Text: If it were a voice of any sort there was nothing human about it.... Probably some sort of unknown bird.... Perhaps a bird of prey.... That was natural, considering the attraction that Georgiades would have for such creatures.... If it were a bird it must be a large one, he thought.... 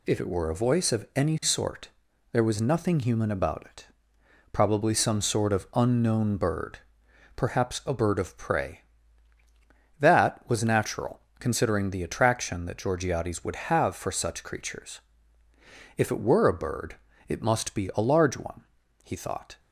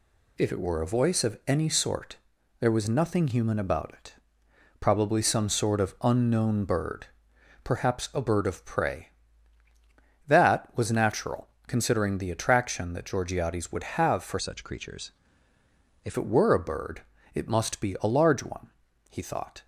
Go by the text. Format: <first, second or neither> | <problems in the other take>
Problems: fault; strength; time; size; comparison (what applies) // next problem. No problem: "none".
first | pauses between "sort" and "there"; at 2.1 s; 0.42 s long; also in the first // changes voice from "such" to "If"; from 14.4 to 16.1 s; 1.7 s long // pauses between "bird" and "it"; slight; at 17.0 s; 0.32 s long; slight in the first